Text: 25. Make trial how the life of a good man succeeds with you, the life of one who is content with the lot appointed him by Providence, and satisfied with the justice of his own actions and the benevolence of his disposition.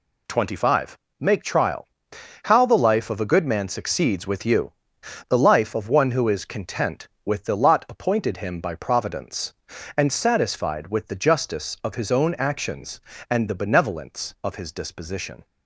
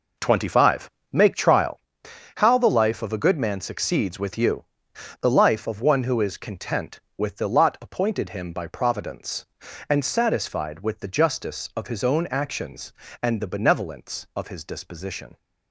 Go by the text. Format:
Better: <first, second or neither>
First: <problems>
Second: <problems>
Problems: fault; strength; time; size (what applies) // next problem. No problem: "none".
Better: first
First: pauses between "trial" and "how"; noticeable; at 1.8 s; 0.58 s long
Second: starts louder than the rest; noticeable; until 1.8 s; 4.5 dB // pauses between "trial" and "how"; noticeable; at 1.7 s; 0.58 s long